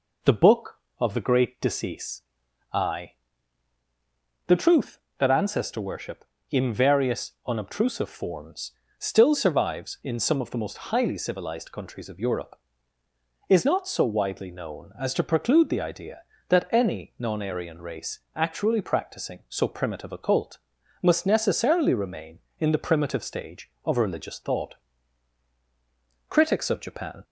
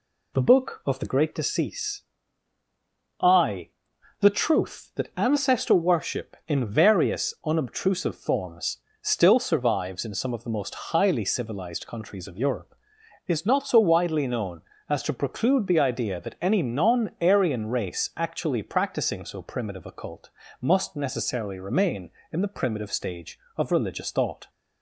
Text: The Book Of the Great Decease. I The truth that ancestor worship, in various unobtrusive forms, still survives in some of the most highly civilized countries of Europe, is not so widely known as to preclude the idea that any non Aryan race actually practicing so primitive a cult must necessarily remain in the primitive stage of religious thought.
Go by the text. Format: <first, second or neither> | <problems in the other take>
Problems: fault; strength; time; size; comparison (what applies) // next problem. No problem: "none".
second | pauses between "I" and "The"; strong; at 3.1 s; 1.3 s long; noticeable in the second // pauses between "various" and "unobtrusive"; slight; at 7.3 s; 0.16 s long // pauses between "race" and "actually"; slight; at 18.1 s; 0.16 s long // pauses between "cult" and "must"; at 20.5 s; 0.42 s long; slight in the second // goes on to say "Critics of Japan"; noticeable; from 26.2 s on; 0.94 s long